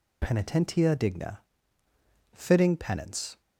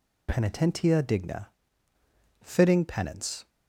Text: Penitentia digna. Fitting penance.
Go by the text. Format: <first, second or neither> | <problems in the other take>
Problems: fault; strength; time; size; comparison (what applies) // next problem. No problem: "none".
neither | none